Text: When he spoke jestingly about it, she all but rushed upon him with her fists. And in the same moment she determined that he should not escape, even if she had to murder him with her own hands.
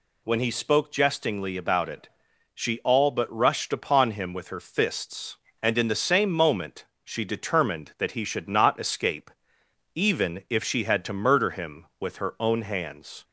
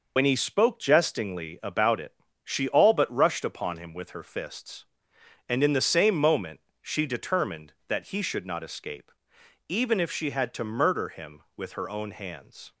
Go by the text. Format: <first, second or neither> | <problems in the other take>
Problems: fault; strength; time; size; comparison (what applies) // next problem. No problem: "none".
first | loses the start of "When"; at 0.1 s; 80 ms // pauses between "moment" and "she"; slight; at 6.6 s; 0.22 s long; slight in the first